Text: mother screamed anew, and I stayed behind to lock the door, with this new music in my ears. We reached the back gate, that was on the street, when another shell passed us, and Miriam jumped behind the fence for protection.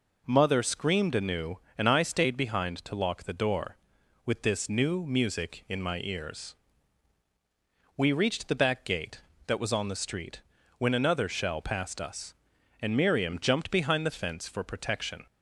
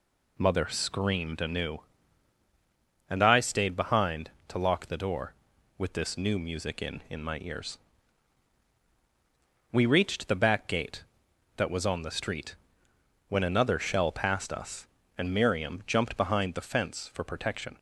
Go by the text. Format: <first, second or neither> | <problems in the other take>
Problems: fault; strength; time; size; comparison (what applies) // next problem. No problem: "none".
first | says "in" twice; at 7.0 s